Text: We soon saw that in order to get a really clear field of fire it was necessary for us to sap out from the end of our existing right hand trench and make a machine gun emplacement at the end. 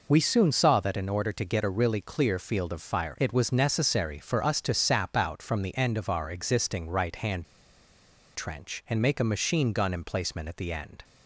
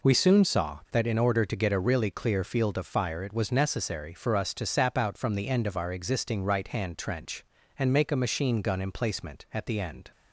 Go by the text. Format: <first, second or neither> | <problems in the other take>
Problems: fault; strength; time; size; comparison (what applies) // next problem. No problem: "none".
second | pauses between "hand" and "trench"; noticeable; at 7.4 s; 0.90 s long